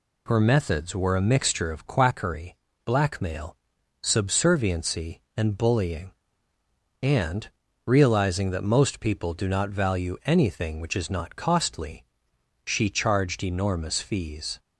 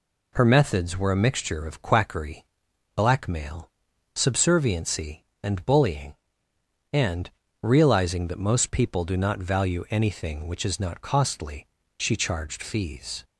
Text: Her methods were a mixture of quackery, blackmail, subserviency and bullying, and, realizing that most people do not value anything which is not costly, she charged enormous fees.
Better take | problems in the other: first | skips "enormous"; at 12.6 s

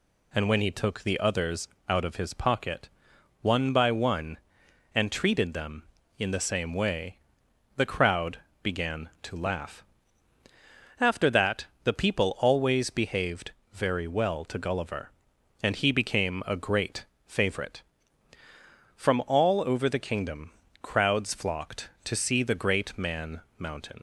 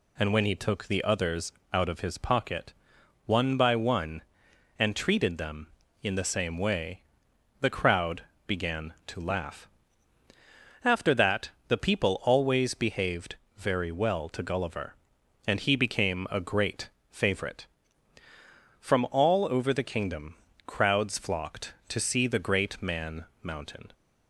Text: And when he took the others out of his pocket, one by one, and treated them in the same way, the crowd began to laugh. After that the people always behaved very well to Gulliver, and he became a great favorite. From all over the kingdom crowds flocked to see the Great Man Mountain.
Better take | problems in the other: second | pauses between "others" and "out"; slight; at 1.6 s; 0.22 s long; slight in the second // pauses between "crowd" and "began"; slight; at 8.3 s; 0.26 s long; slight in the second // pauses between "that" and "the"; slight; at 11.6 s; 0.18 s long; slight in the second // pauses between "behaved" and "very"; slight; at 13.5 s; 0.22 s long; slight in the second // pauses between "great" and "favorite"; slight; at 17.0 s; 0.20 s long; slight in the second // pauses between "kingdom" and "crowds"; slight; at 20.5 s; 0.32 s long; slight in the second // pauses between "Man" and "Mountain"; slight; at 23.4 s; 0.16 s long; slight in the second // leaves "Mountain" unfinished; at 23.9 s; 75 ms

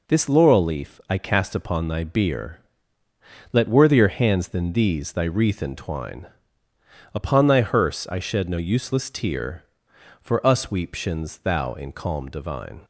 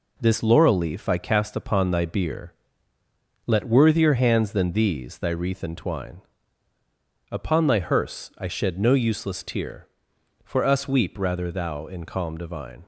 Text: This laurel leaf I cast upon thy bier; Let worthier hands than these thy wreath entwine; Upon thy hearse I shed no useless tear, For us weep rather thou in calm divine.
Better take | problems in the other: second | says "shins" for "rather"; at 10.9 s

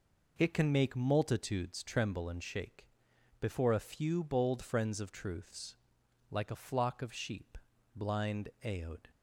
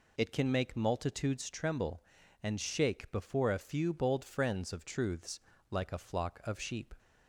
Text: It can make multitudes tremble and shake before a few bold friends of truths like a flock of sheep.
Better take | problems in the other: second | pauses between "shake" and "before"; noticeable; at 2.8 s; 0.54 s long // pauses between "truths" and "like"; noticeable; at 5.7 s; 0.54 s long; slight in the second // goes on to say "Blind aod"; noticeable; from 7.9 s on; 1.1 s long

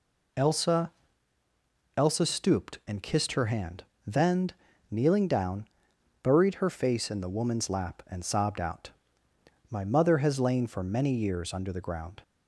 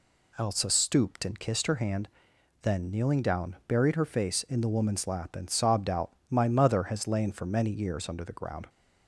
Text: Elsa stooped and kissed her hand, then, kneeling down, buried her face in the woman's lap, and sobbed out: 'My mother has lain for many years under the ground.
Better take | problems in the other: second | says "Elsa" twice; at 1.9 s

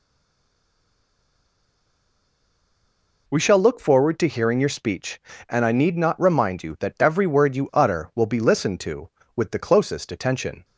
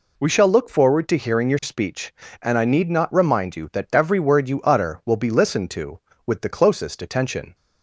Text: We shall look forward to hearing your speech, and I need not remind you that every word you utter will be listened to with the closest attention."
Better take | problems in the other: second | stays silent before the first word; strong; until 3.2 s; 3.2 s long

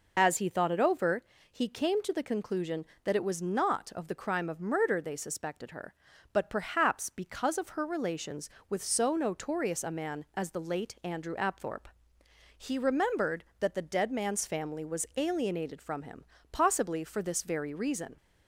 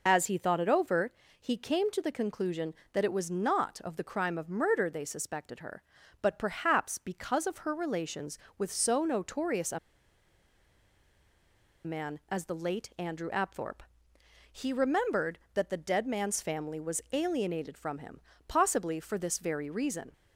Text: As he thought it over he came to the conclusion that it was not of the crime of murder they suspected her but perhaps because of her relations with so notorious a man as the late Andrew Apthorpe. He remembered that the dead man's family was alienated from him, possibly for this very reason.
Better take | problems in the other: first | pauses between "over" and "he"; slight; at 1.1 s; 0.30 s long; slight in the first // pauses between "a" and "man"; strong; at 9.7 s; 2.0 s long

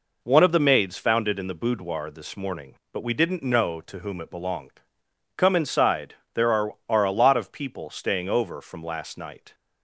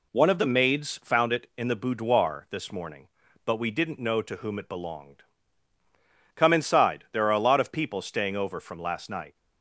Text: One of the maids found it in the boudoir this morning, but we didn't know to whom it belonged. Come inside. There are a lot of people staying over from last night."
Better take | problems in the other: second | says "are" twice; at 6.8 s

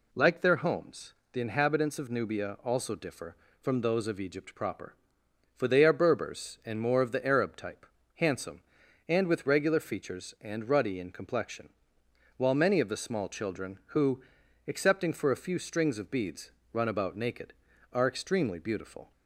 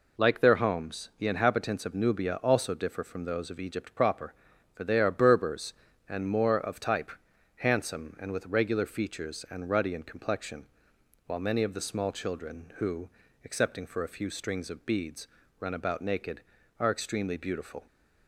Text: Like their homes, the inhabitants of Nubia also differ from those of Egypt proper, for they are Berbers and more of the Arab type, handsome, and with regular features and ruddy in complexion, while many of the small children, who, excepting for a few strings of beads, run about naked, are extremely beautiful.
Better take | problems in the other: first | skips "the Arab"; at 6.7 s

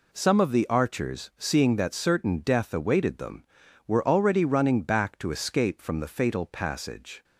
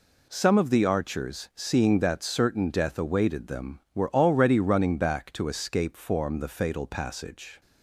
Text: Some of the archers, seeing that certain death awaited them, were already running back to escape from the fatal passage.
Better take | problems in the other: first | says "form" for "from"; at 5.9 s

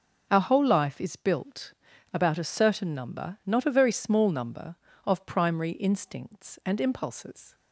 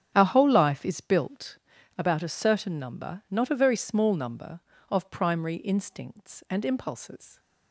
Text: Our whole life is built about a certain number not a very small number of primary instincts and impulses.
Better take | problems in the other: first | starts louder than the rest; strong; until 1.5 s; 8.5 dB // pauses between "built" and "about"; at 1.5 s; 0.40 s long; also in the first

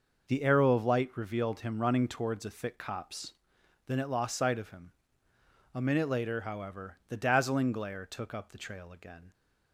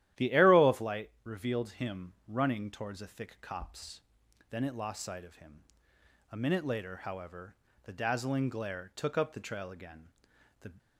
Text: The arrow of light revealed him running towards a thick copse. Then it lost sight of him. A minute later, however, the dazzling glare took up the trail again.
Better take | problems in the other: first | starts louder than the rest; strong; until 1.3 s; 12.5 dB // goes on to say "The"; slight; from 10.6 s on; 0.10 s long

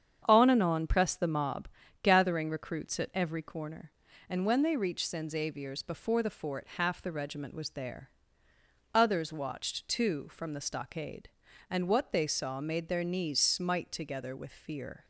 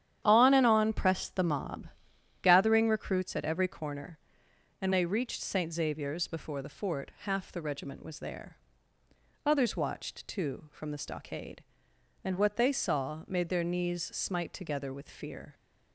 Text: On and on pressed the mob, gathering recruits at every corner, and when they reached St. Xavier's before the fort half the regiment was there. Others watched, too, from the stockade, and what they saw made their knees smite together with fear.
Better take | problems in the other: first | starts louder than the rest; strong; until 1.2 s; 10 dB; strong in the first // skips "when"; at 4.9 s

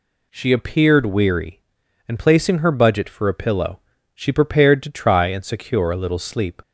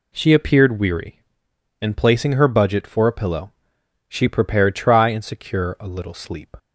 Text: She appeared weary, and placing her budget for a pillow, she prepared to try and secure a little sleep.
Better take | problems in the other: first | skips "to"; at 4.7 s

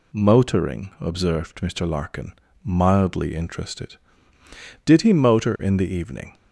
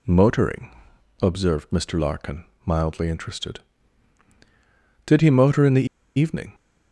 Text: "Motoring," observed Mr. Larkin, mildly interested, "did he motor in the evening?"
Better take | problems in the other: first | pauses between "the" and "evening"; slight; at 5.8 s; 0.31 s long

